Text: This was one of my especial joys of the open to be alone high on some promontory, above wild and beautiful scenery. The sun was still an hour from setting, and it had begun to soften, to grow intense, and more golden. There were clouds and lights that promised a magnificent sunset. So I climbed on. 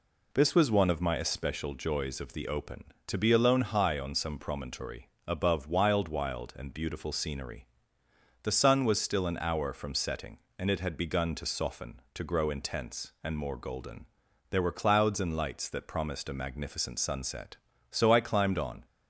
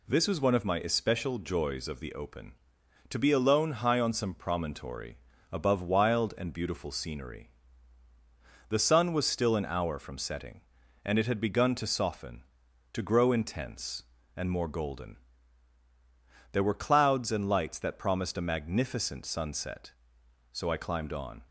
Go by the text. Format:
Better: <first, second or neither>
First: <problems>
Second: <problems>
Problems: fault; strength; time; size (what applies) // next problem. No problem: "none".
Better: second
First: says "wild" twice; at 6.0 s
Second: none